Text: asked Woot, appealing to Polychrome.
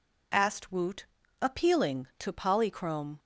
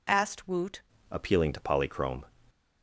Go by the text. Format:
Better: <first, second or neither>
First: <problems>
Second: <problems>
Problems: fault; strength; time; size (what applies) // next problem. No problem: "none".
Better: first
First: none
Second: changes voice at "appealing"; from 1.1 s on; 1.1 s long